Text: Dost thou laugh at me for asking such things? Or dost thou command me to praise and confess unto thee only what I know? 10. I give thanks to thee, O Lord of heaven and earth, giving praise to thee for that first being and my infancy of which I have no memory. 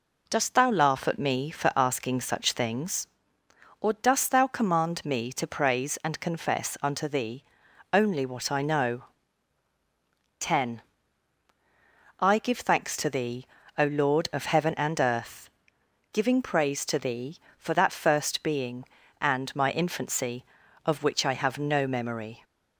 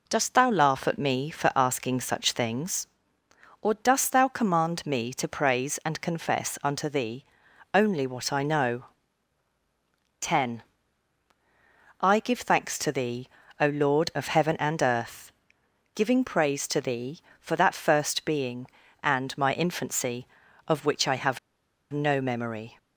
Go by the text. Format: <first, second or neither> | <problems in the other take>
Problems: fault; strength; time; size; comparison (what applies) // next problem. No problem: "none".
first | pauses between "thee" and "only"; noticeable; at 7.2 s; 0.50 s long; noticeable in the first // pauses between "have" and "no"; noticeable; at 21.3 s; 0.52 s long